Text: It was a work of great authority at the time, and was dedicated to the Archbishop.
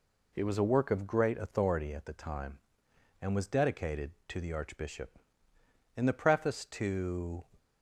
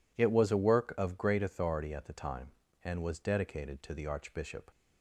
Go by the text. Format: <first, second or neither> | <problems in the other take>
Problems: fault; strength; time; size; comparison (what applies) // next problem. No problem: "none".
second | goes on to say "In the preface to"; from 5.9 s on; 1.4 s long